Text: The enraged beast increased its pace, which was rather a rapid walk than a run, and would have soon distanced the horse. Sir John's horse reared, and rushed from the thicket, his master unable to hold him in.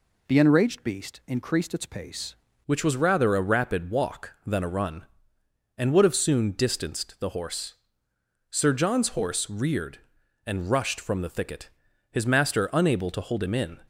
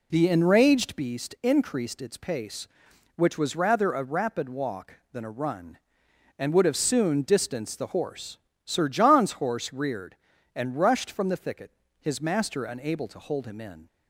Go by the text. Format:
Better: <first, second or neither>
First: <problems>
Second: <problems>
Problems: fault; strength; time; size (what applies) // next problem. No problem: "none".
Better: second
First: changes voice at "which"; from 2.6 s on; 11.2 s long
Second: none